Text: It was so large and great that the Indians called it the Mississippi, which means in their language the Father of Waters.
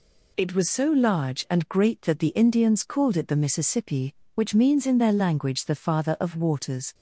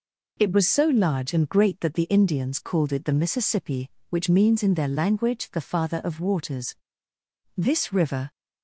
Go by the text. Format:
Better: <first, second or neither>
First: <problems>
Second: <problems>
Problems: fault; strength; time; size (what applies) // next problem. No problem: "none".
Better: first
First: none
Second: goes on to say "This river"; noticeable; from 7.5 s on; 0.74 s long